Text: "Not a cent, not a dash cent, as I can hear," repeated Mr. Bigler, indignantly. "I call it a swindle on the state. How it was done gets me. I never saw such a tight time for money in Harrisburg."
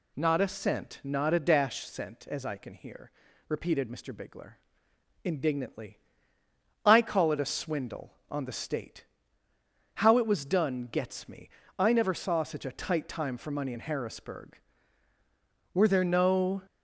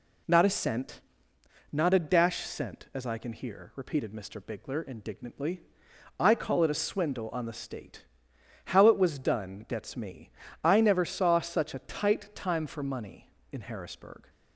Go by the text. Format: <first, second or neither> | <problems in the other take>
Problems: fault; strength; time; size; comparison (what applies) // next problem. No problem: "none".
second | goes on to say "Were there no"; noticeable; from 15.7 s on; 0.90 s long